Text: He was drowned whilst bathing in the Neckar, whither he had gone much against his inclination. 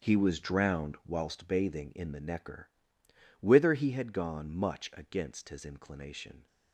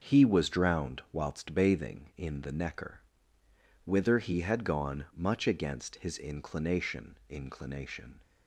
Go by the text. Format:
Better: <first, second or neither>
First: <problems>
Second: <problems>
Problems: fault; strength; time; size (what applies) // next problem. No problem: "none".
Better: first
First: starts louder than the rest; strong; until 1.1 s; 7.5 dB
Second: starts louder than the rest; until 1.1 s; 6.5 dB // says "inclination" twice; at 7.2 s